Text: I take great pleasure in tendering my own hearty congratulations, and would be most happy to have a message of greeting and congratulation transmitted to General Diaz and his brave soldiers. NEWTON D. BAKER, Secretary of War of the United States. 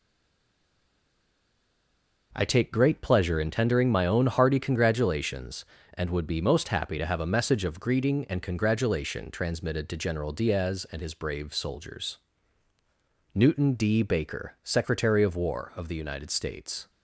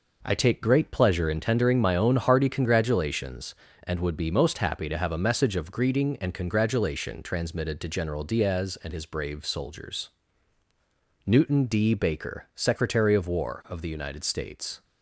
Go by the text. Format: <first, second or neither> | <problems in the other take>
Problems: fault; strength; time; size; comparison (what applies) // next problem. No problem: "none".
second | stays silent before the first word; until 2.3 s; 2.3 s long